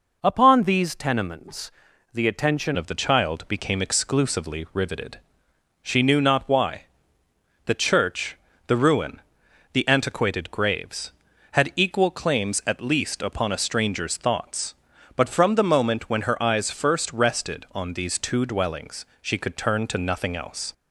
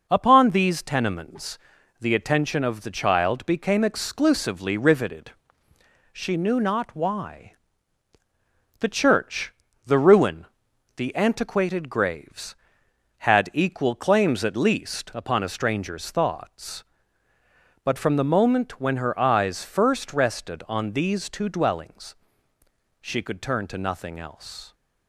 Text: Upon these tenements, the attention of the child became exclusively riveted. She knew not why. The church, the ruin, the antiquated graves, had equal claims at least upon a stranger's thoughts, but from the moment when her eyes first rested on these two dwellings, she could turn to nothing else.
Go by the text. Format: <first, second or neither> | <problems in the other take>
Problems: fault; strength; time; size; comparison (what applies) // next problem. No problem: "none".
second | changes voice at "of"; from 2.7 s on; 18.0 s long